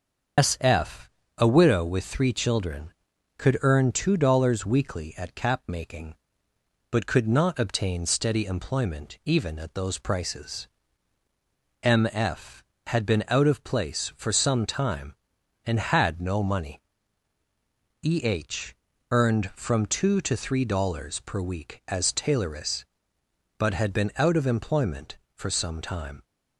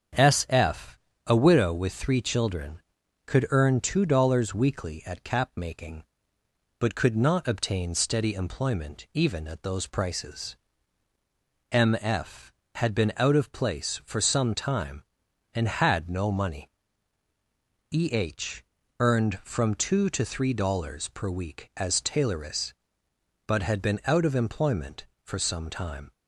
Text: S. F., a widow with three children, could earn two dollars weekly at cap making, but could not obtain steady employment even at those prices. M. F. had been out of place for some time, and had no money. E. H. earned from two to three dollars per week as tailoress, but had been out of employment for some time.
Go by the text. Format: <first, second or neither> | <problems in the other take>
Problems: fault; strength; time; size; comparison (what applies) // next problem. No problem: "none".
second | loses the start of "S"; at 0.3 s; 135 ms // starts louder than the rest; until 1.6 s; 6 dB; also in the second // pauses between "H" and "earned"; slight; at 18.7 s; 0.36 s long; slight in the second